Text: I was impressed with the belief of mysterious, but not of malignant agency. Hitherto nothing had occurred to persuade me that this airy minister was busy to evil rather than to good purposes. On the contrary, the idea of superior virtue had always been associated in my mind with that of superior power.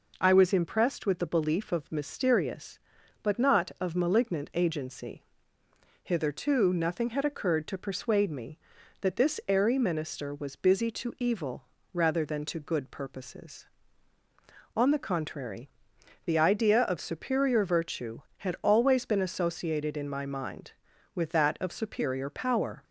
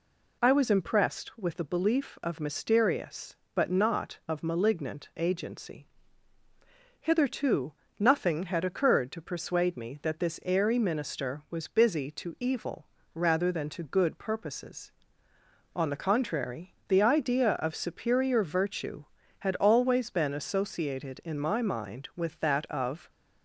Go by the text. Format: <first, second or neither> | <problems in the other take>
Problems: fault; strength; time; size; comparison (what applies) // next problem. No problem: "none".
first | pauses between "Hitherto" and "nothing"; slight; at 7.7 s; 0.26 s long // pauses between "evil" and "rather"; slight; at 12.8 s; 0.28 s long; slight in the first // stops before "superior power"; at 23.0 s